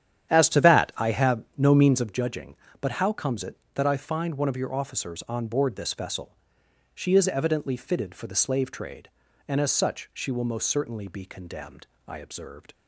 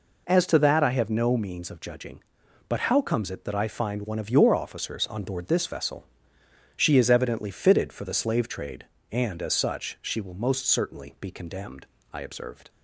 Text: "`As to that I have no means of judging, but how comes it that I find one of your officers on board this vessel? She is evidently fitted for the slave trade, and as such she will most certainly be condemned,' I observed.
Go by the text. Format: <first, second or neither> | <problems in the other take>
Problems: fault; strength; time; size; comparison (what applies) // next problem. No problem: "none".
second | starts louder than the rest; strong; until 2.2 s; 10 dB